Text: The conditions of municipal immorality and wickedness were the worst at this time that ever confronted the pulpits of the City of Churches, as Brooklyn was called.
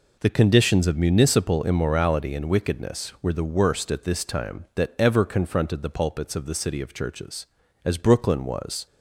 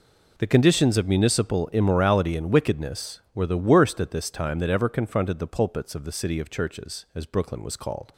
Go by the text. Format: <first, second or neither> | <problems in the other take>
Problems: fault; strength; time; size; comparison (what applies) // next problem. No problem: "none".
second | stops before "called"; at 8.8 s